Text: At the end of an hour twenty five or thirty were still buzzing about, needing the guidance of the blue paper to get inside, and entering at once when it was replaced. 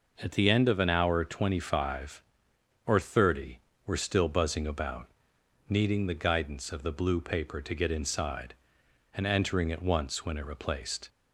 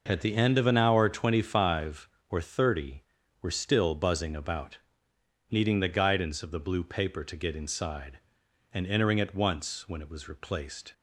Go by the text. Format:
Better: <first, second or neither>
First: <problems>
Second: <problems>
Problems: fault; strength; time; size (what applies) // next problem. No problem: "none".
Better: second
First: skips "was"; at 10.4 s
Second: none